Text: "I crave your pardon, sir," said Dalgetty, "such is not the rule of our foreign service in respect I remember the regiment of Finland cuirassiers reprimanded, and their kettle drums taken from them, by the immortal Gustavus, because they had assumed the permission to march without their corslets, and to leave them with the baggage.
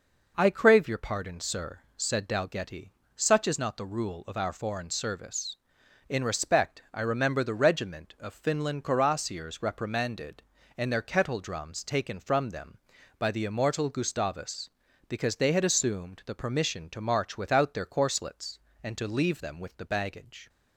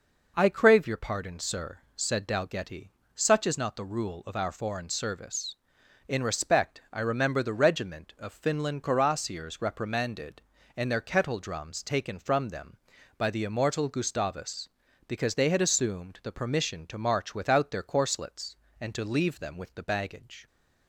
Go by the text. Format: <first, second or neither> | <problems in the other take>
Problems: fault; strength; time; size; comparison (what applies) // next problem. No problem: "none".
neither | none